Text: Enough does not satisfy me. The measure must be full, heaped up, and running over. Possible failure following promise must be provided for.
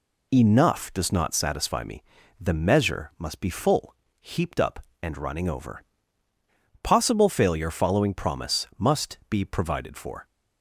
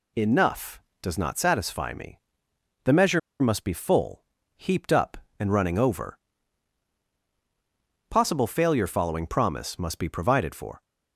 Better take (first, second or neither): first